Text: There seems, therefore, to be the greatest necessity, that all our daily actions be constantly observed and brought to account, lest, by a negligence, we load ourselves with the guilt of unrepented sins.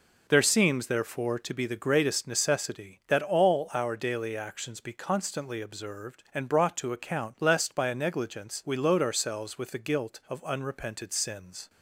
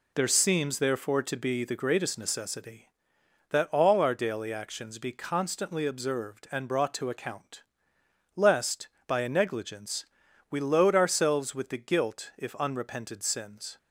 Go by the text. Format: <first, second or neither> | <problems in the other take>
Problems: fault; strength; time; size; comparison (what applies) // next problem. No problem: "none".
first | says "if" for "of"; at 12.3 s